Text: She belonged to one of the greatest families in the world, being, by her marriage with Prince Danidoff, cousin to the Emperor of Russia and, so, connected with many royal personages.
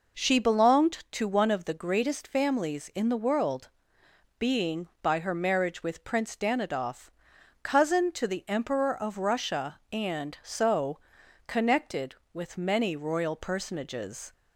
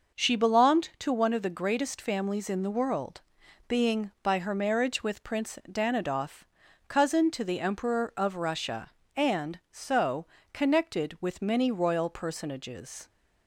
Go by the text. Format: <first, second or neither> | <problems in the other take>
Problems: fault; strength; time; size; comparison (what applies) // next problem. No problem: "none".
neither | none